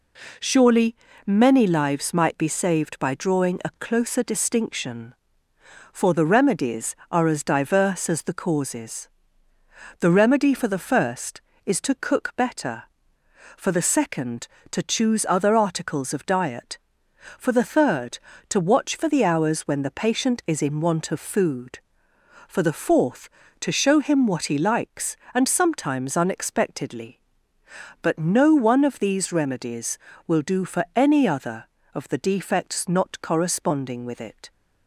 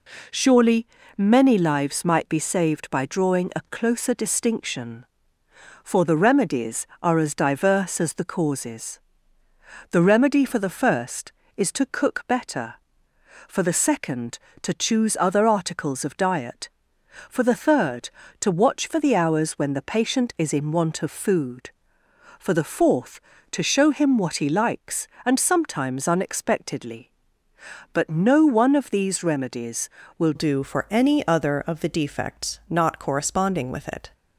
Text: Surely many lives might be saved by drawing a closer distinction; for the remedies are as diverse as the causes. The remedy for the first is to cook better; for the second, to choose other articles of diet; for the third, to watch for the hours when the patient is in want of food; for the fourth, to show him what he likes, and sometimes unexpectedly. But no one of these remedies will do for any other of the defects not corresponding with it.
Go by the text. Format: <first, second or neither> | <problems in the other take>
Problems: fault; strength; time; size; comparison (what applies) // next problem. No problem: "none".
first | pauses between "Surely" and "many"; slight; at 0.8 s; 0.28 s long; slight in the first // changes voice at "do"; from 30.3 s on; 3.8 s long